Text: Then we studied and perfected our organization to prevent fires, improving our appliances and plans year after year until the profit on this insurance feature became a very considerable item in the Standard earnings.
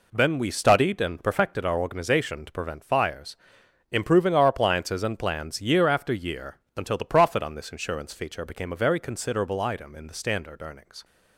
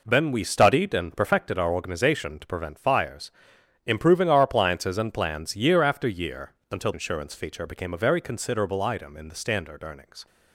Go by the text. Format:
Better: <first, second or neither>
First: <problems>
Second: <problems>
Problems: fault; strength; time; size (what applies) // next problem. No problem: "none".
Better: first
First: pauses between "year" and "until"; slight; at 6.5 s; 0.18 s long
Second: pauses between "year" and "until"; slight; at 6.5 s; 0.18 s long // skips "the profit on this"; at 6.9 s